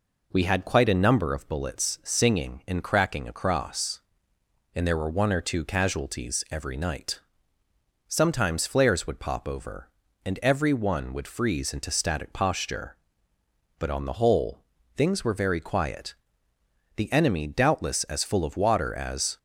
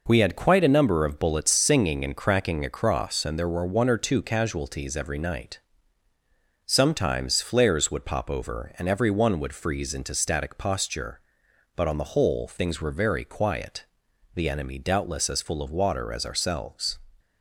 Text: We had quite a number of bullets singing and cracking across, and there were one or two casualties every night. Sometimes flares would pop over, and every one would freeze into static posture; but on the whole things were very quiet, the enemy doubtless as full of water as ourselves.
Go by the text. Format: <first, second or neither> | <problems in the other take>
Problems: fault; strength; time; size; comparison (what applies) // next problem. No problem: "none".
second | pauses between "whole" and "things"; slight; at 14.6 s; 0.32 s long // stops before "ourselves"; at 19.3 s